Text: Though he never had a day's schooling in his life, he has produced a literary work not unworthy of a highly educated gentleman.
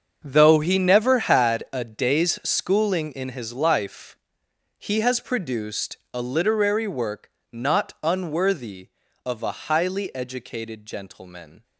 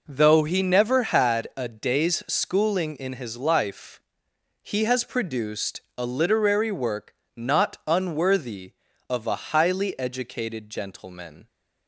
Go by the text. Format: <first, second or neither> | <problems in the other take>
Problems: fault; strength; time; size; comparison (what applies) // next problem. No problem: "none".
second | gets quieter; strong; throughout; 14 dB // pauses between "produced" and "a"; slight; at 5.9 s; 0.16 s long; slight in the second // pauses between "work" and "not"; slight; at 7.2 s; 0.22 s long; slight in the second